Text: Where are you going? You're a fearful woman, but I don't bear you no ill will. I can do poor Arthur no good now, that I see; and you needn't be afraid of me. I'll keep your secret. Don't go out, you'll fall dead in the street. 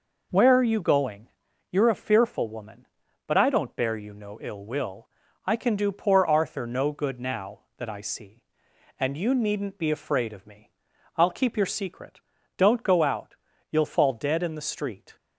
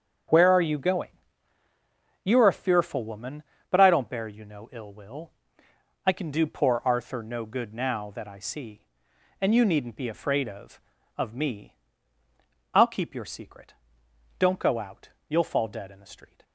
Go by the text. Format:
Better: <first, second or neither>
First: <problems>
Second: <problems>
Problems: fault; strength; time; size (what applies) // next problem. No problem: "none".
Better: first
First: none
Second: starts louder than the rest; strong; until 2.4 s; 7.5 dB // says "of" twice; at 11.1 s